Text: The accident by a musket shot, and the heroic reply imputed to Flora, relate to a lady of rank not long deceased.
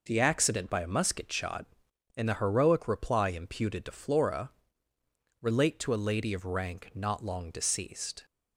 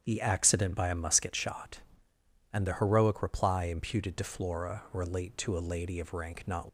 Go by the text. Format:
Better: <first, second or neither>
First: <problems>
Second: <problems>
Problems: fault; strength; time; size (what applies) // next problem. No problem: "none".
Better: first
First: none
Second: starts louder than the rest; strong; until 1.0 s; 8.5 dB // stops before "long deceased"; at 6.6 s